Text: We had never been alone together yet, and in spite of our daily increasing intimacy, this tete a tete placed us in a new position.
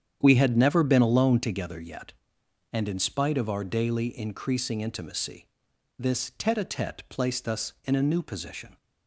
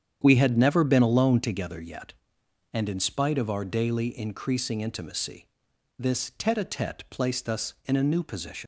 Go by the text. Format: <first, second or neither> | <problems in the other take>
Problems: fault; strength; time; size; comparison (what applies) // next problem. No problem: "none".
first | starts louder than the rest; strong; until 1.2 s; 8.5 dB; strong in the first // leaves "position" unfinished; at 8.6 s; 120 ms